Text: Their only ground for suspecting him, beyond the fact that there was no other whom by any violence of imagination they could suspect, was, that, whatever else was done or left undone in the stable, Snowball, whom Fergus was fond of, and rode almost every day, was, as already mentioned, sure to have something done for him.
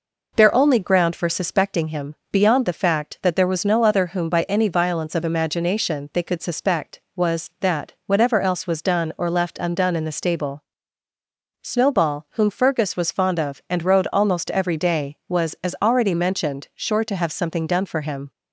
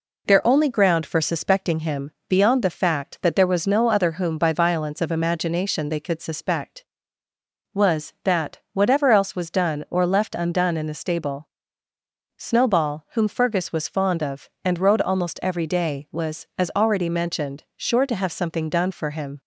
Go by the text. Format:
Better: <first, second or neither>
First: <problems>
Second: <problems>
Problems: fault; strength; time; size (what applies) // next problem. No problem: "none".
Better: first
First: none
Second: skips "any"; at 4.5 s